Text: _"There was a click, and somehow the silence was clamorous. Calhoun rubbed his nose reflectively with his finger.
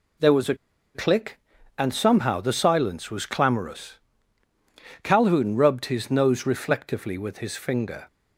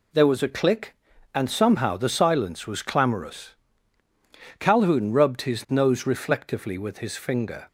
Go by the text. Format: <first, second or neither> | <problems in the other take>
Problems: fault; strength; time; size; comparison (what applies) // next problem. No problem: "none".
second | pauses between "a" and "click"; at 0.5 s; 0.39 s long